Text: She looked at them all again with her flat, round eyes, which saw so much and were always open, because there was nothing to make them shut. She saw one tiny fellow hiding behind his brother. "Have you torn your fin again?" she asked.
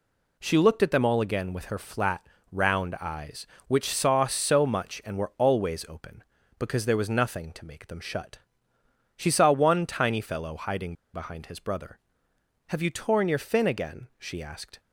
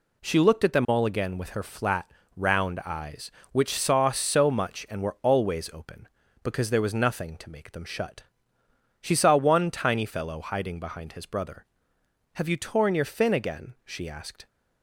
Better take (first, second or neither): second